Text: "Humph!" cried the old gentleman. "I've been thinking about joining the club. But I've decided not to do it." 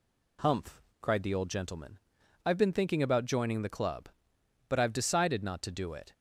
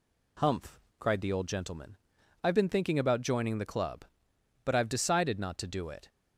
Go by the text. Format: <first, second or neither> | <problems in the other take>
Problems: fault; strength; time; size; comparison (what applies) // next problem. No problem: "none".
neither | none